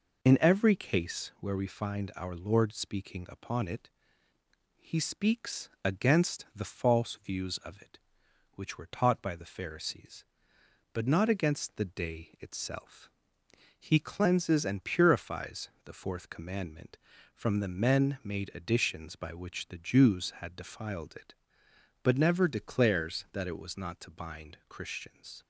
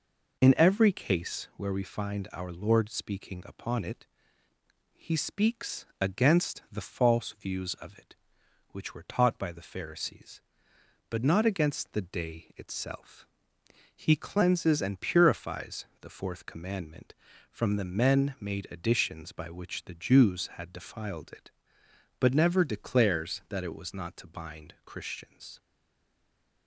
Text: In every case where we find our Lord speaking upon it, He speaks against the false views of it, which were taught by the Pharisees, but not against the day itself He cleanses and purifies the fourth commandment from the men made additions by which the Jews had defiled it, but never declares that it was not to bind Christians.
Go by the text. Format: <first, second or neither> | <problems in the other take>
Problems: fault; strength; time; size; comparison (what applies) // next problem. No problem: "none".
first | pauses between "speaks" and "against"; slight; at 5.8 s; 0.16 s long; slight in the first // pauses between "itself" and "He"; noticeable; at 13.2 s; 0.70 s long; noticeable in the first // pauses between "purifies" and "the"; slight; at 15.8 s; 0.16 s long; slight in the first // stays silent after the last word; from 25.5 s on; 1.1 s long